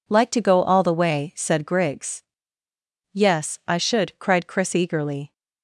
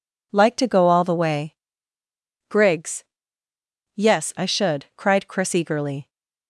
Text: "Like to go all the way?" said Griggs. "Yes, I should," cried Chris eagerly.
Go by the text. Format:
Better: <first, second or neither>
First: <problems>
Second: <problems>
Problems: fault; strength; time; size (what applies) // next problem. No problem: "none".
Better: first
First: none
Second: skips "said"; at 2.0 s